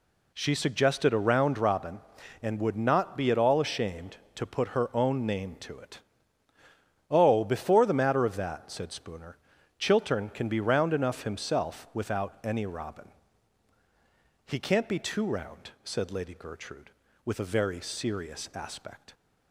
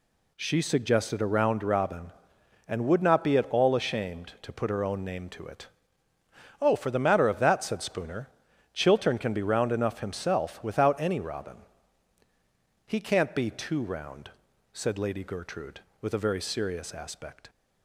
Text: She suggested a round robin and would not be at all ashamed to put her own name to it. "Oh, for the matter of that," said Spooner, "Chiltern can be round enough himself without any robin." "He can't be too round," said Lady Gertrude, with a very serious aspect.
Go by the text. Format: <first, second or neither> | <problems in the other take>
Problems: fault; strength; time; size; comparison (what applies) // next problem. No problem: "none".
second | says "before" for "for"; at 7.4 s